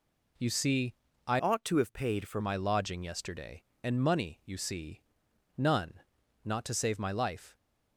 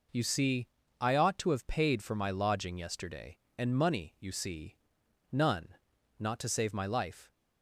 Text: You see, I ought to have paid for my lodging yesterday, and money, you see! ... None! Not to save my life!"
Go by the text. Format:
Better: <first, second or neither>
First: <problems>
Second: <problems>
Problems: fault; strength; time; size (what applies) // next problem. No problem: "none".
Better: second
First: changes voice from "ought" to "for"; from 1.3 to 2.4 s; 1.1 s long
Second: none